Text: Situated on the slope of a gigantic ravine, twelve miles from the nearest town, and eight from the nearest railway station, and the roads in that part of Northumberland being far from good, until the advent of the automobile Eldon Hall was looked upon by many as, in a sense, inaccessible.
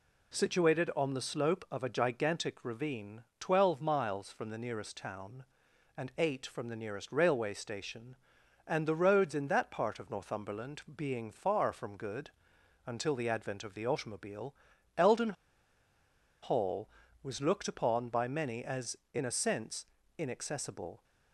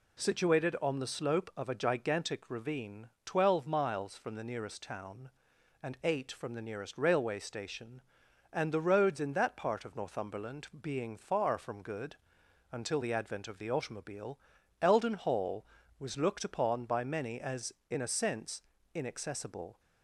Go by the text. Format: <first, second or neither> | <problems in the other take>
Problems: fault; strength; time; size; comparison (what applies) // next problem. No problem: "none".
second | pauses between "Northumberland" and "being"; slight; at 10.8 s; 0.16 s long; slight in the second // pauses between "automobile" and "Eldon"; at 14.5 s; 0.42 s long; also in the second // pauses between "Eldon" and "Hall"; at 15.3 s; 1.0 s long